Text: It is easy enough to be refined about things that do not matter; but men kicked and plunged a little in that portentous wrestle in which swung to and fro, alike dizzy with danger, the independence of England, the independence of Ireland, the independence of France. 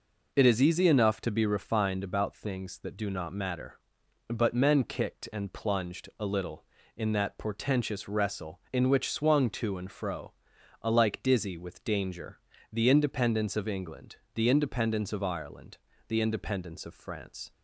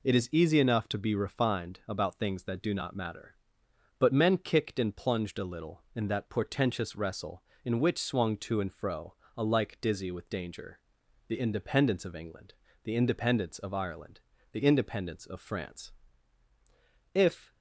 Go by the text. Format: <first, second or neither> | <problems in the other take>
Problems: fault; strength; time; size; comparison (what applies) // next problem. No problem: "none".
first | goes on to say "If"; slight; from 17.1 s on; 0.40 s long